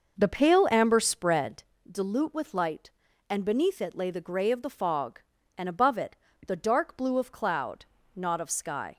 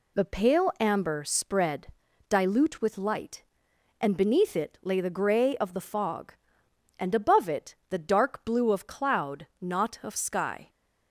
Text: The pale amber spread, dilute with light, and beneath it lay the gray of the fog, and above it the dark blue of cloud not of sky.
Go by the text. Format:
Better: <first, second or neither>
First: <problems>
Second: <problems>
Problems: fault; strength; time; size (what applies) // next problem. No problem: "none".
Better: second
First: starts louder than the rest; noticeable; until 1.7 s; 5.5 dB // pauses between "it" and "the"; slight; at 6.1 s; 0.30 s long // pauses between "cloud" and "not"; slight; at 7.8 s; 0.30 s long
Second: pauses between "it" and "the"; slight; at 7.7 s; 0.16 s long